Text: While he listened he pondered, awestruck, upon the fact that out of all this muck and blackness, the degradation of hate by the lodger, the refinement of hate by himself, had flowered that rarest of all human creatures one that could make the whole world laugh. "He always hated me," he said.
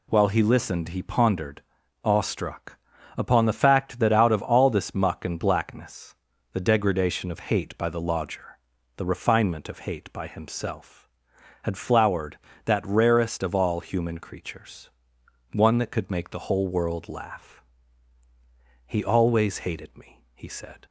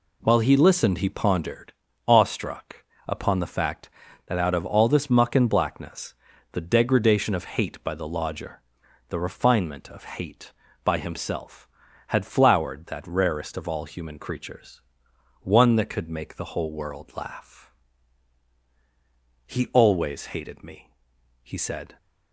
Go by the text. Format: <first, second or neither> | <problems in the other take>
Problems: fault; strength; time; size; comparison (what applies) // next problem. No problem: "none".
neither | pauses between "creatures" and "one"; noticeable; the same in both